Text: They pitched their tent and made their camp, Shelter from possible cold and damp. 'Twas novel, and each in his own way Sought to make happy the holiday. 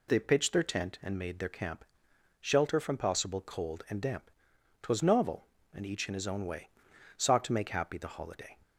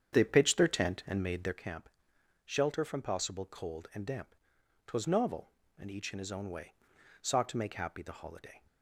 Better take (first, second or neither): first